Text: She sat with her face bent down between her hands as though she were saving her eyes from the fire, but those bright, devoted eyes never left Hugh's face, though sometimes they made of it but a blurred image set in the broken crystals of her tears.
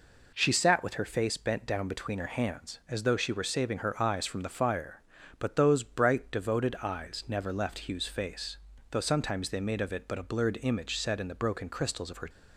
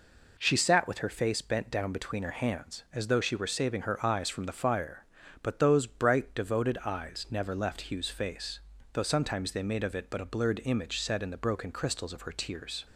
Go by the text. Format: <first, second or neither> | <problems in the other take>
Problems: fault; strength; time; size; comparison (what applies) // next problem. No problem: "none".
second | stops before "tears"; at 12.2 s